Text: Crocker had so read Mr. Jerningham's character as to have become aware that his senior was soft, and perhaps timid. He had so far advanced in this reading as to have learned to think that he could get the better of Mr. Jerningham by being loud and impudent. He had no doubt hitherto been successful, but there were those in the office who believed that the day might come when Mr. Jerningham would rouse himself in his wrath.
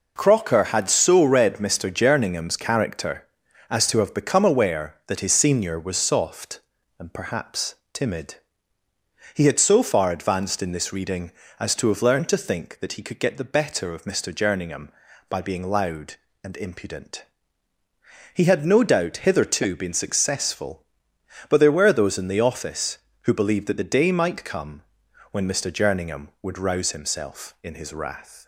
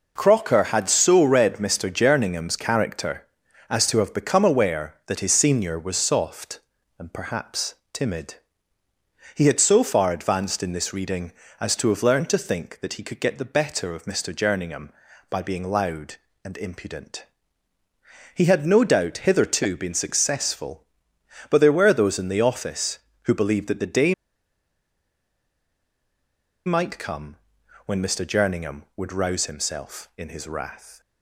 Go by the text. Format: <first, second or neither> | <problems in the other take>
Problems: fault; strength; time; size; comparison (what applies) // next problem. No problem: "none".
first | pauses between "perhaps" and "timid"; slight; at 7.7 s; 0.18 s long; slight in the first // pauses between "day" and "might"; strong; at 24.1 s; 2.5 s long // pauses between "come" and "when"; noticeable; at 27.3 s; 0.50 s long; noticeable in the first